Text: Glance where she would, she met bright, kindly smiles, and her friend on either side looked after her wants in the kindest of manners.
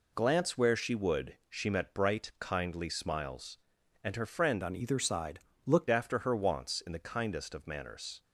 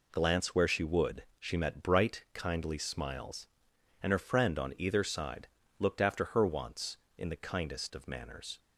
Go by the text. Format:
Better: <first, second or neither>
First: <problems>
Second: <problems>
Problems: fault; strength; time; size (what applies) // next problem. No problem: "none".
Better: second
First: changes voice from "on" to "looked"; from 4.6 to 5.8 s; 1.2 s long // pauses between "side" and "looked"; slight; at 5.3 s; 0.26 s long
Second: pauses between "side" and "looked"; slight; at 5.4 s; 0.30 s long